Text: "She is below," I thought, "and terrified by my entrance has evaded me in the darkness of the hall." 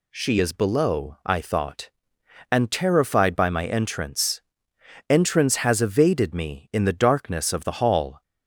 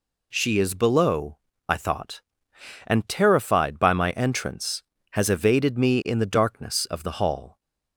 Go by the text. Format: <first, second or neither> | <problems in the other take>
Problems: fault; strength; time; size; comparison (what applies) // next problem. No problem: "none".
second | says "entrance" twice; at 5.1 s